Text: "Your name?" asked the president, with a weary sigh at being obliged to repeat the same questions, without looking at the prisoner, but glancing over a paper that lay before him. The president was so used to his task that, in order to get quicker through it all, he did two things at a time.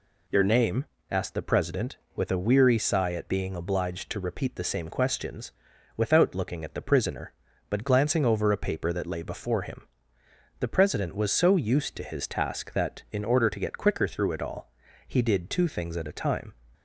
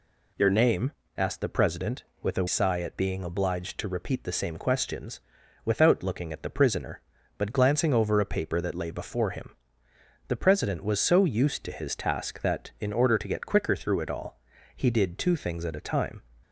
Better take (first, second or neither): first